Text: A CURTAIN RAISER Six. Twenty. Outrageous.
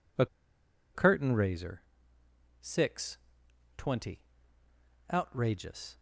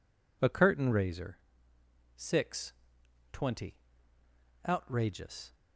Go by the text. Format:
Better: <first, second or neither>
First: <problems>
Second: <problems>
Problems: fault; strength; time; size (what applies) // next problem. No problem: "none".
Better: second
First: pauses between "A" and "CURTAIN"; noticeable; at 0.2 s; 0.67 s long // pauses between "RAISER" and "Six"; noticeable; at 1.8 s; 0.80 s long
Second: pauses between "RAISER" and "Six"; noticeable; at 1.3 s; 0.79 s long